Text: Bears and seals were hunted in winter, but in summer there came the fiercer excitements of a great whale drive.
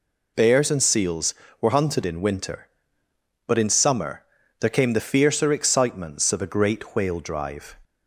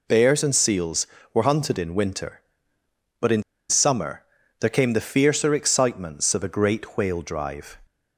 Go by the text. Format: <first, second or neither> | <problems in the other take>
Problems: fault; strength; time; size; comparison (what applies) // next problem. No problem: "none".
first | pauses between "in" and "summer"; slight; at 3.4 s; 0.26 s long // pauses between "summer" and "there"; slight; at 4.2 s; 0.36 s long; slight in the first